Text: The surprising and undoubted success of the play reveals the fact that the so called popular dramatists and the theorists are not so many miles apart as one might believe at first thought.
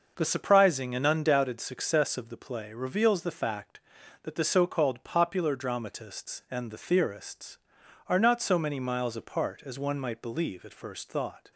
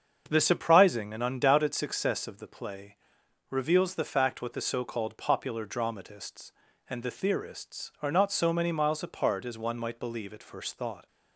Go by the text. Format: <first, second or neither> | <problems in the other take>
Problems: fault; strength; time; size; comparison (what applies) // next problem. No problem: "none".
first | starts louder than the rest; until 1.2 s; 7 dB // pauses between "play" and "reveals"; noticeable; at 2.9 s; 0.52 s long // says "what" for "that"; at 4.4 s